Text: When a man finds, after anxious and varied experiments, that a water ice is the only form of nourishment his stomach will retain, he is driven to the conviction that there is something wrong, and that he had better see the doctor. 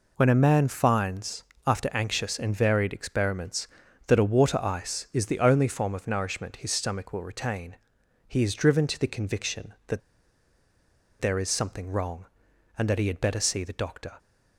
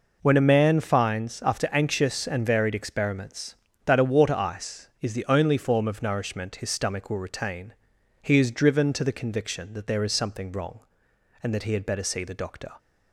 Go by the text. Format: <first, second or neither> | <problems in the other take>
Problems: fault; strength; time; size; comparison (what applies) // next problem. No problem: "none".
second | pauses between "that" and "there"; at 10.0 s; 1.2 s long